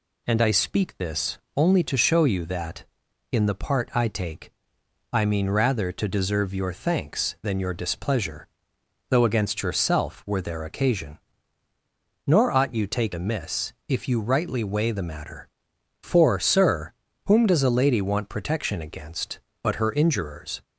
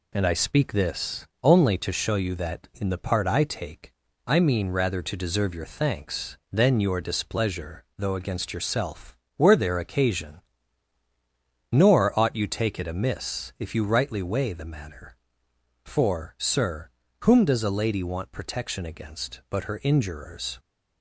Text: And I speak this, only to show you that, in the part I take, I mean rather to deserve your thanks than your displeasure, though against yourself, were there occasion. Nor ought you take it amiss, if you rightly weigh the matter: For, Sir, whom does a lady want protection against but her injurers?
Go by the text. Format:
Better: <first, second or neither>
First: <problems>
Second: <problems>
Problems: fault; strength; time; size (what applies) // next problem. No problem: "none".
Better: second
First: skips "it"; at 13.1 s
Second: none